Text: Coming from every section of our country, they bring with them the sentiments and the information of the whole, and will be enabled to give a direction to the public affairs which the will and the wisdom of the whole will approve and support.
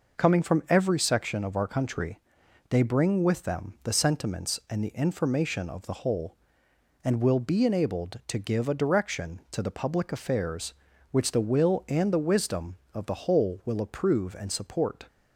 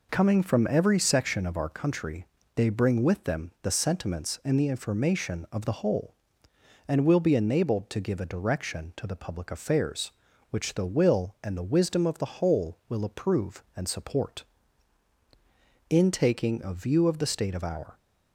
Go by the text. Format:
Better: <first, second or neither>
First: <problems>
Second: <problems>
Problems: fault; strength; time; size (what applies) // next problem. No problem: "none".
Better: first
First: none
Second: goes on to say "In taking a view of the state of our"; strong; from 15.8 s on; 2.0 s long